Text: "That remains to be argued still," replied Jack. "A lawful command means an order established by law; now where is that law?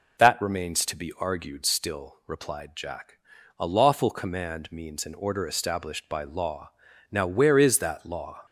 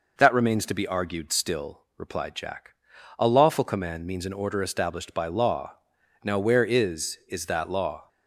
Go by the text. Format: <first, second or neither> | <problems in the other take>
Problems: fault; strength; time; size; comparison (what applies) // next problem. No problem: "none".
first | says "is" twice; at 7.2 s